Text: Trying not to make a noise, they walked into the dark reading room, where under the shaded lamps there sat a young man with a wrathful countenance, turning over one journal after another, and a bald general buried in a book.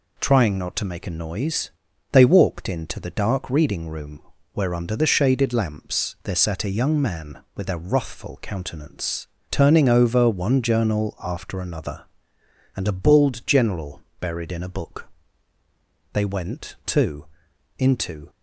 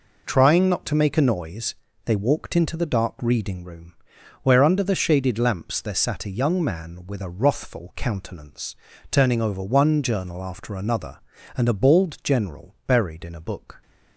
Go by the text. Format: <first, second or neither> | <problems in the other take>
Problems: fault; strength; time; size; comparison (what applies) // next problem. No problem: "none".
second | pauses between "general" and "buried"; slight; at 14.0 s; 0.18 s long // goes on to say "They went too into"; strong; from 16.1 s on; 2.1 s long